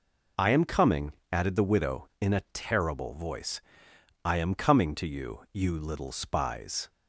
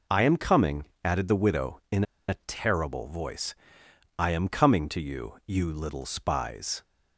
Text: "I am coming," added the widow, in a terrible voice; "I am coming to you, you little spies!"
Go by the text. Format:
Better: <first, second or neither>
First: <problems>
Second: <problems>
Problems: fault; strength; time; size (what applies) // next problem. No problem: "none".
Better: first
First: none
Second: pauses between "in" and "a"; slight; at 2.0 s; 0.23 s long